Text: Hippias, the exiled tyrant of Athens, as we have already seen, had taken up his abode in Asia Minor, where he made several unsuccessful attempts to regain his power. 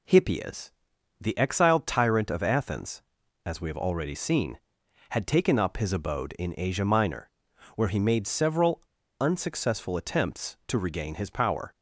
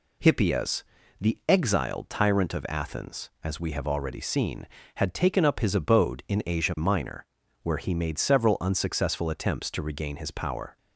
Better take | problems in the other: second | pauses between "several" and "unsuccessful"; at 8.8 s; 0.39 s long

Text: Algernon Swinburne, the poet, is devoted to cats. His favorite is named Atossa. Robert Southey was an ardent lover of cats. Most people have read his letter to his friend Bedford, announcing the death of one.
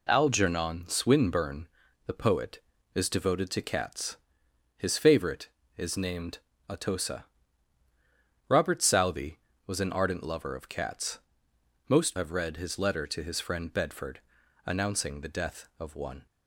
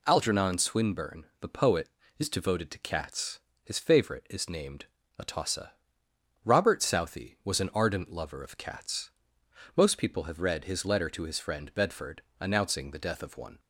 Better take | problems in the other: second | pauses between "named" and "Atossa"; slight; at 6.3 s; 0.32 s long; slight in the second // skips "people"; at 12.1 s

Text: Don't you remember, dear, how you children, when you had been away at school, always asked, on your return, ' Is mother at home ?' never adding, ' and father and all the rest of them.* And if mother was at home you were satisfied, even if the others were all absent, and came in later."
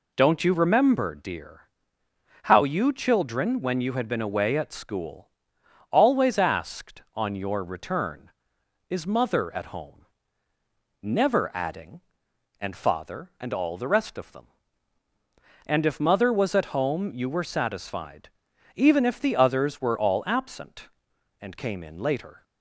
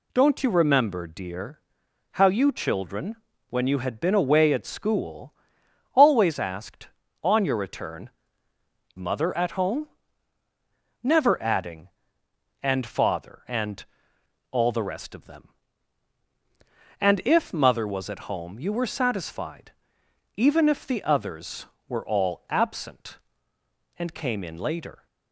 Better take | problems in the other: first | skips "Is"; at 8.9 s // pauses between "and" and "all"; noticeable; at 13.8 s; 0.66 s long

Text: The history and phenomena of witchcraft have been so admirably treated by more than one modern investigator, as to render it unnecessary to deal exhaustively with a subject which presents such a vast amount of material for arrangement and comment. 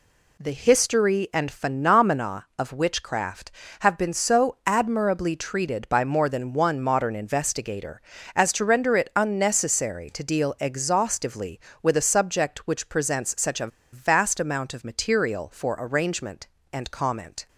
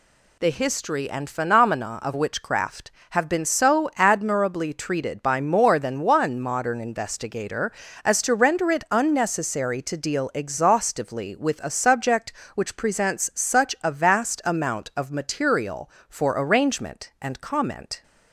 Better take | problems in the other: second | pauses between "a" and "vast"; slight; at 13.6 s; 0.25 s long

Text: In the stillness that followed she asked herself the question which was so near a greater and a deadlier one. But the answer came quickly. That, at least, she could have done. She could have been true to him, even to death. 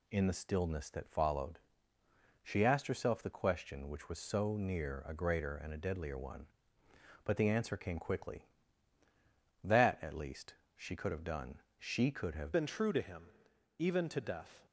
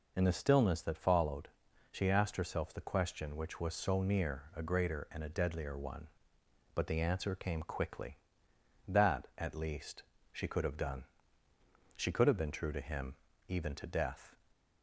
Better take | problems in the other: second | pauses between "followed" and "she"; noticeable; at 1.5 s; 0.86 s long; also in the second // changes voice at "been"; from 12.5 s on; 2.1 s long

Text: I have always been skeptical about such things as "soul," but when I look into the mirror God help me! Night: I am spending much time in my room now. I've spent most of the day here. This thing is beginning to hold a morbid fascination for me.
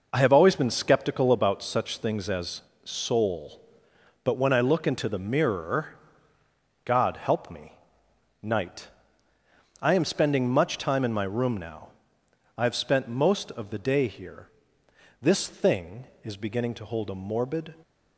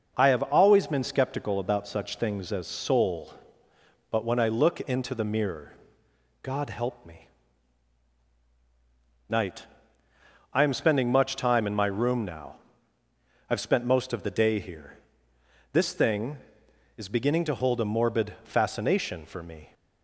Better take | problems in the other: second | pauses between "as" and "soul"; slight; at 2.6 s; 0.20 s long // pauses between "mirror" and "God"; noticeable; at 5.9 s; 0.88 s long; noticeable in the second // stops before "fascination for me"; at 17.8 s

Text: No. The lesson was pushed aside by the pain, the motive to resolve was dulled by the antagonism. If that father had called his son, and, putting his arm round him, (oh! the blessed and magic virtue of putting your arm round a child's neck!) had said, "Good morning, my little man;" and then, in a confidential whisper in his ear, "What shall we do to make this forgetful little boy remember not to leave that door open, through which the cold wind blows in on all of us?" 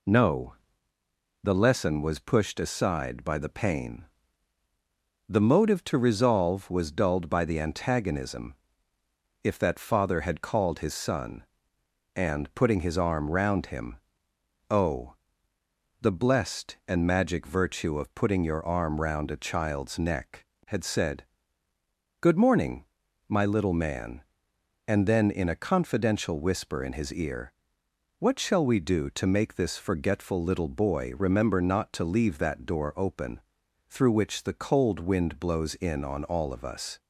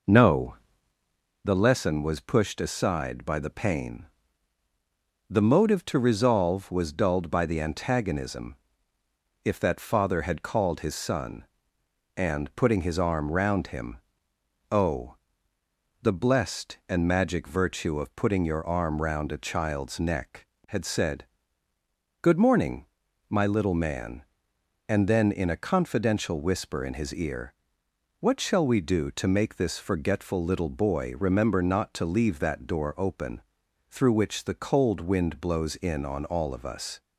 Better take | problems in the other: first | starts louder than the rest; noticeable; until 1.5 s; 5 dB

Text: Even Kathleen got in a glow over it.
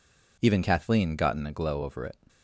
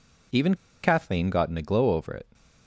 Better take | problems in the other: first | pauses between "Even" and "Kathleen"; slight; at 0.5 s; 0.28 s long

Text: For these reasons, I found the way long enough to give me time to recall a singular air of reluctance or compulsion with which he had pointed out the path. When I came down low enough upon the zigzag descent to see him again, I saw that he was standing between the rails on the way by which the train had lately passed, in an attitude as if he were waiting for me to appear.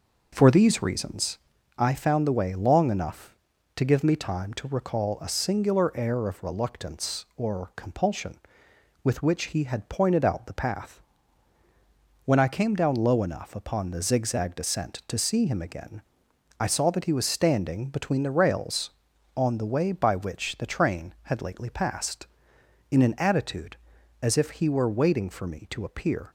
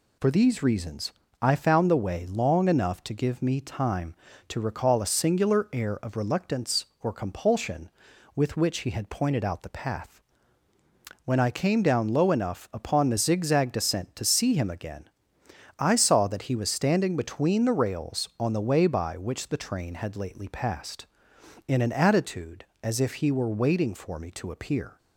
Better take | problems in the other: second | starts louder than the rest; noticeable; until 1.6 s; 5.5 dB

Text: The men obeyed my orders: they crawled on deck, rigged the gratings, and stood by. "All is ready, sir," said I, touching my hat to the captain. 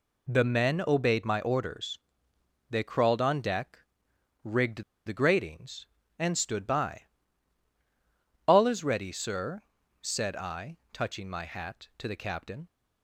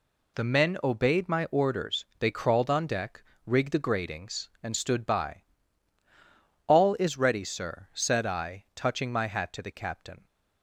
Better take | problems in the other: second | pauses between "rigged" and "the"; slight; at 4.8 s; 0.23 s long

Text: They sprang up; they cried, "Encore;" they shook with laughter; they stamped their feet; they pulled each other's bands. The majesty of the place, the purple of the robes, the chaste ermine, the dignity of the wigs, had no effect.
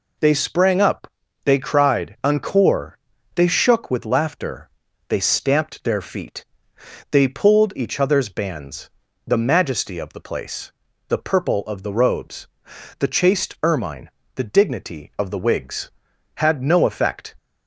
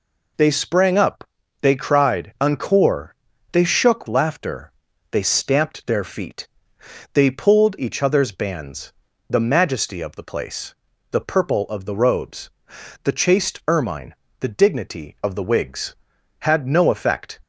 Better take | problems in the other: first | skips "with"; at 4.0 s

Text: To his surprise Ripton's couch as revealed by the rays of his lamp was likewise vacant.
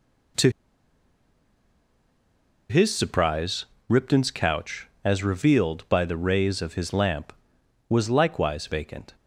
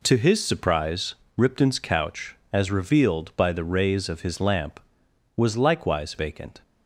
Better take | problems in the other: second | pauses between "To" and "his"; strong; at 0.4 s; 2.2 s long // pauses between "surprise" and "Ripton's"; slight; at 3.6 s; 0.24 s long; slight in the second

